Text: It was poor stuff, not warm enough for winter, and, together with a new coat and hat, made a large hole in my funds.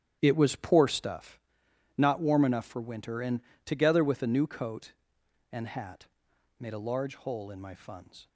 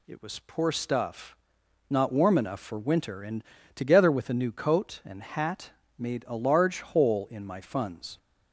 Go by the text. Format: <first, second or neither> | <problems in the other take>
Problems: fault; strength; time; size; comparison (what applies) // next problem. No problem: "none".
second | starts louder than the rest; strong; until 1.2 s; 10 dB